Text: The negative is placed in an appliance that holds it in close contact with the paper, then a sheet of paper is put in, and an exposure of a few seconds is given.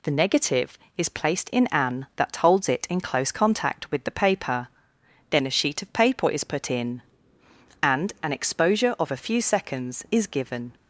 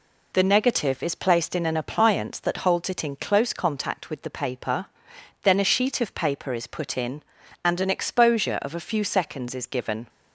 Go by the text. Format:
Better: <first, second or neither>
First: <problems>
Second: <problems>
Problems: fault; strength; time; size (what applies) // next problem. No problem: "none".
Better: second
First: skips "appliance"; at 2.1 s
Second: none